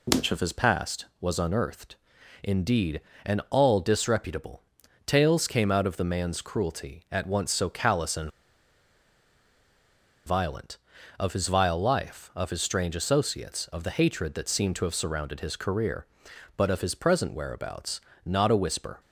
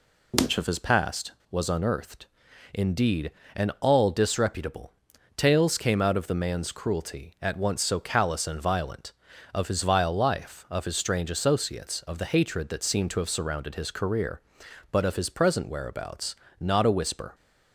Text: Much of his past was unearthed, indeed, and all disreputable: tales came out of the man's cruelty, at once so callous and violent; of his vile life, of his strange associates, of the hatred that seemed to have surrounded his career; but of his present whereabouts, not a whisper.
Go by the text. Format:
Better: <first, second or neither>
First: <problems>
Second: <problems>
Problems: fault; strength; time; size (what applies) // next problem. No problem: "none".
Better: second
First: pauses between "and" and "violent"; strong; at 8.3 s; 1.9 s long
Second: none